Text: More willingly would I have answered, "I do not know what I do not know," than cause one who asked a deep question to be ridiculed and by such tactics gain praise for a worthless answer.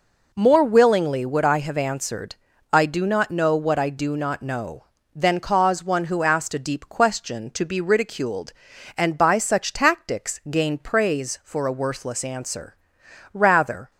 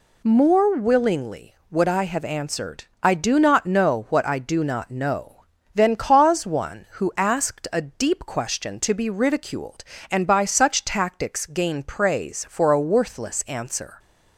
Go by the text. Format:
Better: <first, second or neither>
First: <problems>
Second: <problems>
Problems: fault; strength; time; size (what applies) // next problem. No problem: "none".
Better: second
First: goes on to say "Rather"; from 13.3 s on; 0.56 s long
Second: none